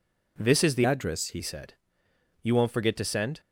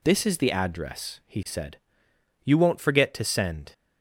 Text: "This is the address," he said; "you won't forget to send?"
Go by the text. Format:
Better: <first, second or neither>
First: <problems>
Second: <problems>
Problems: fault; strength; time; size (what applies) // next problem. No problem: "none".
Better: second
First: changes voice from "address" to "he"; from 0.8 to 1.4 s; 0.6 s long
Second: none